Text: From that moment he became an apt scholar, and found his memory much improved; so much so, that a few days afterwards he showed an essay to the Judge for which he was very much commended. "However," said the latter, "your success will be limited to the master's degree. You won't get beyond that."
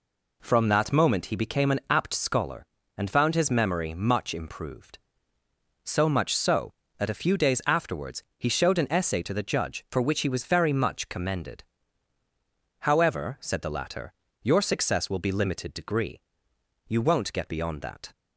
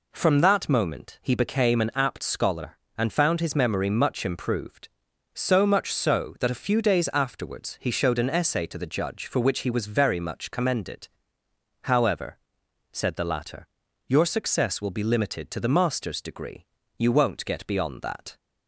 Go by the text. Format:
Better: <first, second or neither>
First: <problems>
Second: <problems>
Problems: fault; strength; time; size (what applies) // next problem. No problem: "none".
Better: second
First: pauses between "afterwards" and "he"; slight; at 8.2 s; 0.16 s long // skips "to the master's"; at 15.7 s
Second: none